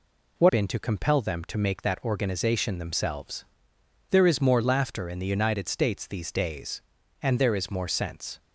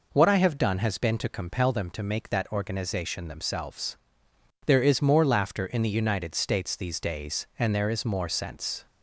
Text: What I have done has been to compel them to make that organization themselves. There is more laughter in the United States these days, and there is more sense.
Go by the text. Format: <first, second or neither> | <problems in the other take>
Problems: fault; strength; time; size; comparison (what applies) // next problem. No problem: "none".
second | skips "I have done has"; at 0.4 s